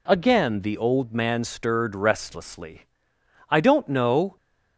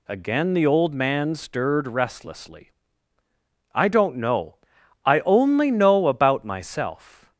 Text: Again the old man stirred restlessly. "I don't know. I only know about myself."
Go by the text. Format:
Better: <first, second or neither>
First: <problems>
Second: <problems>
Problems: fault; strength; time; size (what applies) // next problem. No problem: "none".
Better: second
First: stops before "I only know about myself"; at 4.3 s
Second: none